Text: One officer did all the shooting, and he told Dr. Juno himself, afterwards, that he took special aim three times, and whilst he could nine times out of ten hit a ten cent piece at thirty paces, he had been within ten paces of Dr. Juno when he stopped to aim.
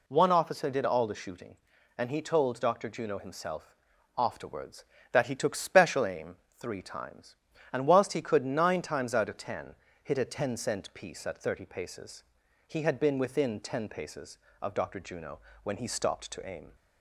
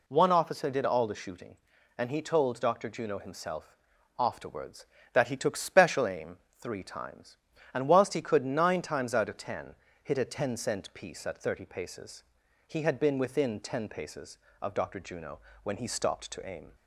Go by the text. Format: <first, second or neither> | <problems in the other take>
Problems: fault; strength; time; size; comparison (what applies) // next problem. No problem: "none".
neither | pauses between "aim" and "three"; slight; the same in both // pauses between "ten" and "hit"; slight; the same in both // pauses between "Juno" and "when"; slight; the same in both